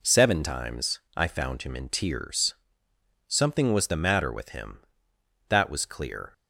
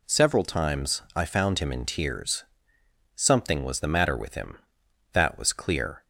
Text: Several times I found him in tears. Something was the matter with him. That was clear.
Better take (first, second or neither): second